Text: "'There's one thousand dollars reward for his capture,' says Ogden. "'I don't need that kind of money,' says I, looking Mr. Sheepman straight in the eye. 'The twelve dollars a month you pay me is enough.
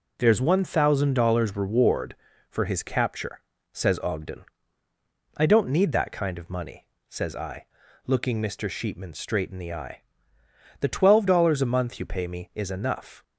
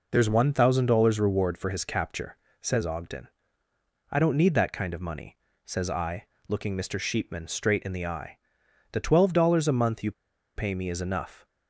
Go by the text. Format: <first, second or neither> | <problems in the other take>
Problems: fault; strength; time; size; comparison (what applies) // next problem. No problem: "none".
first | pauses between "you" and "pay"; at 10.1 s; 0.44 s long